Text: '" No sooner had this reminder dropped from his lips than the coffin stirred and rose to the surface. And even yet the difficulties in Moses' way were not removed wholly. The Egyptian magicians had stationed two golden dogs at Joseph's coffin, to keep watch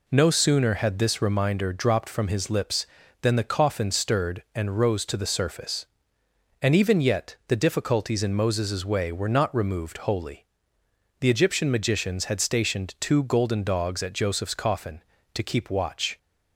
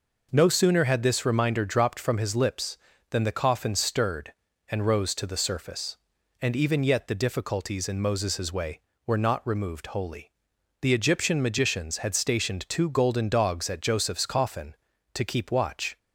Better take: neither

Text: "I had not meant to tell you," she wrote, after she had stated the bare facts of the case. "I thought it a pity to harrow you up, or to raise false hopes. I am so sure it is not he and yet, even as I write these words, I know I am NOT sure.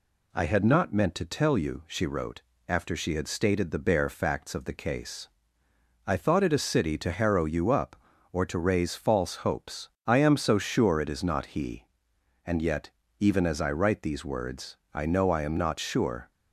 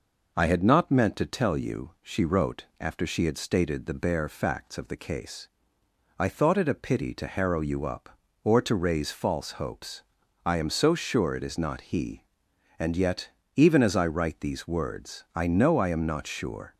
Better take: second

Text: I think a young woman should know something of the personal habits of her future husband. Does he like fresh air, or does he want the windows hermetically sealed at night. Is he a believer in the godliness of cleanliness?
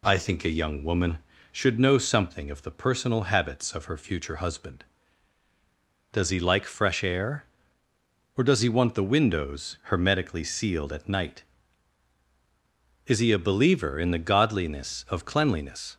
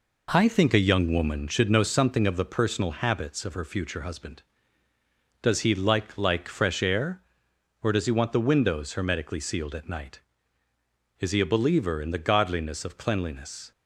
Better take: first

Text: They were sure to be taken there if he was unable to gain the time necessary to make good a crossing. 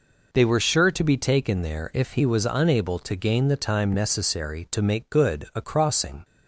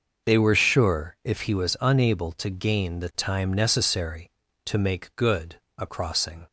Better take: first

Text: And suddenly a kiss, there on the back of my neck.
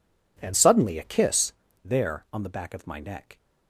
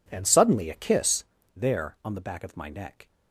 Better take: neither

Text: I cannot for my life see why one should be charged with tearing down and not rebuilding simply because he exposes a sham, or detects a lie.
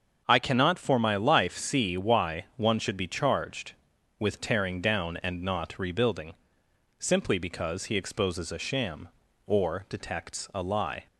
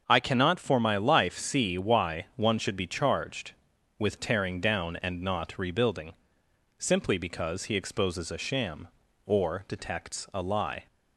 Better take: neither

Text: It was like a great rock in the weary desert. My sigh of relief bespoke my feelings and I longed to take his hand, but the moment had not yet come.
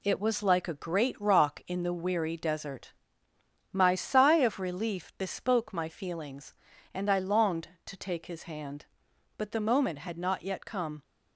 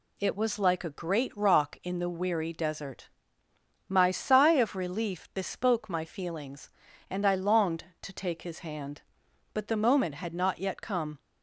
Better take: second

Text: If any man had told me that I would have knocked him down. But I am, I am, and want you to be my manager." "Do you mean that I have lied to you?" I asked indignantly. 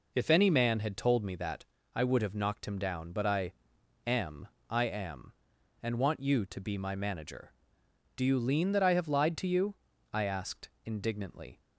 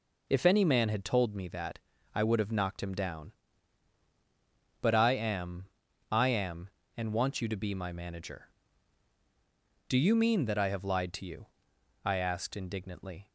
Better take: second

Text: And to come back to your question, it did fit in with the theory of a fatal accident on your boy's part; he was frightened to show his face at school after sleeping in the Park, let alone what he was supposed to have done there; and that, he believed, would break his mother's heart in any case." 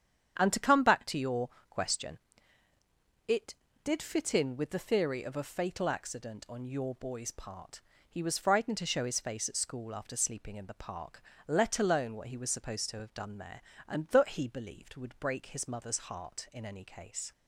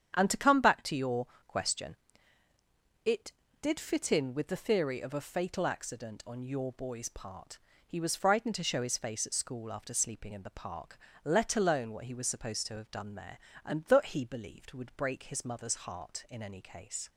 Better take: neither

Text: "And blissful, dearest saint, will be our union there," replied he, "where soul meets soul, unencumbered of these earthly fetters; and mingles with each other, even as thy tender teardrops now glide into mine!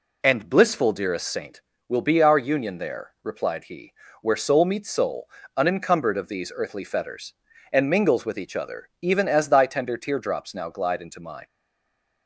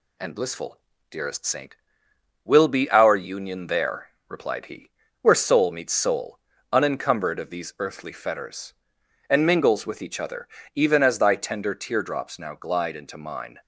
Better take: second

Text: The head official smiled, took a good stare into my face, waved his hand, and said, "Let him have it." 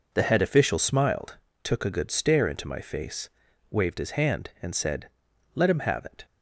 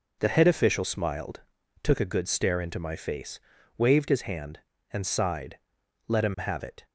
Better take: first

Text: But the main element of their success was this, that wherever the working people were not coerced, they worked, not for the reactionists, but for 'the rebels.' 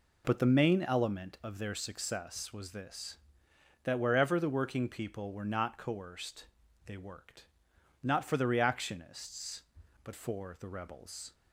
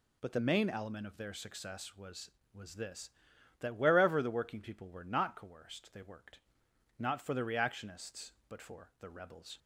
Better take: first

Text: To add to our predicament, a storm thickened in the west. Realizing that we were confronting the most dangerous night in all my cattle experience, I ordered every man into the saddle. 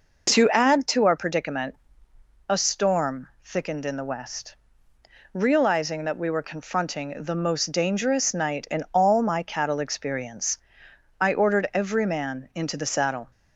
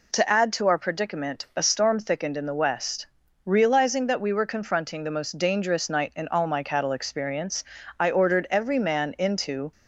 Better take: first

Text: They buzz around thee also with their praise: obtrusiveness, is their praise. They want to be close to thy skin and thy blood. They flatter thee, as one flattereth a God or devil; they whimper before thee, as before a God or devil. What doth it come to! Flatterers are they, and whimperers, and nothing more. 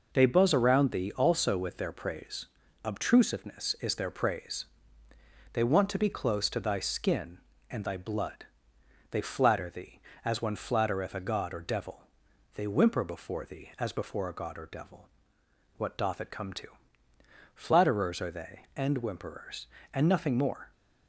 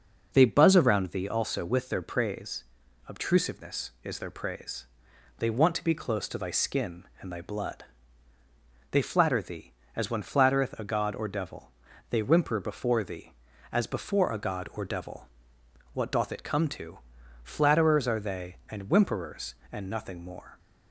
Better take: neither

